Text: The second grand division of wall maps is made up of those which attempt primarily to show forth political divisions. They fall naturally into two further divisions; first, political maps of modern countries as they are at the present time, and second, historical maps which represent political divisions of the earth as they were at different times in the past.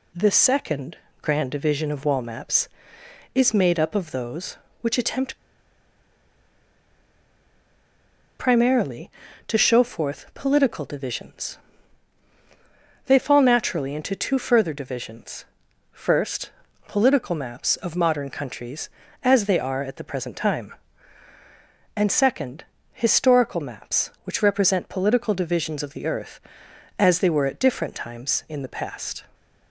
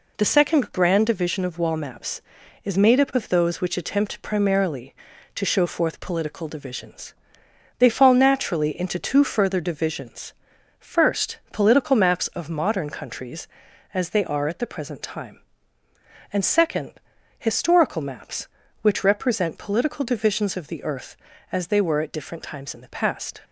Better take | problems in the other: second | pauses between "second" and "grand"; slight; at 0.9 s; 0.24 s long // pauses between "attempt" and "primarily"; strong; at 5.3 s; 3.0 s long

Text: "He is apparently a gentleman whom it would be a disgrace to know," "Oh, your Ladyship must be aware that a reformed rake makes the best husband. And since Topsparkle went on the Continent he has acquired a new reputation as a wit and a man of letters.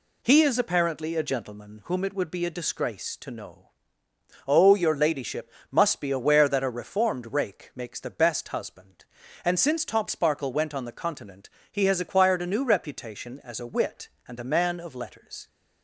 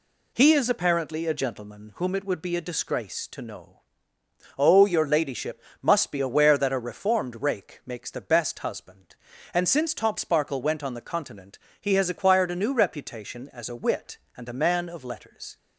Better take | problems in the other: neither | pauses between "Ladyship" and "must"; slight; the same in both // pauses between "Continent" and "he"; slight; the same in both

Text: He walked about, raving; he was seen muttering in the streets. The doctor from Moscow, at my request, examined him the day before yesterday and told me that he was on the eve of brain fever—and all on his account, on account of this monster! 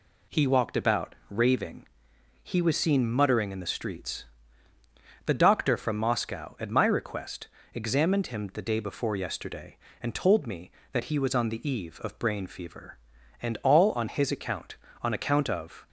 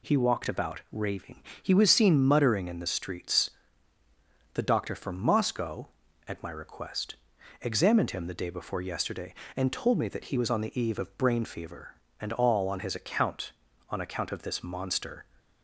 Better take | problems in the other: second | stops before "this monster"; at 15.8 s

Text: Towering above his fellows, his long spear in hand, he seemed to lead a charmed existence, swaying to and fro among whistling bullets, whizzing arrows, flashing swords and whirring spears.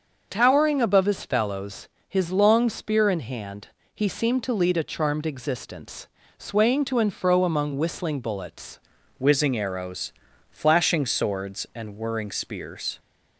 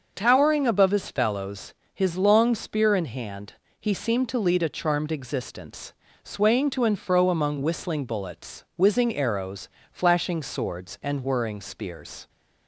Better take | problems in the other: second | starts louder than the rest; until 1.3 s; 6 dB; also in the second // changes voice at "whizzing"; from 9.1 s on; 3.8 s long

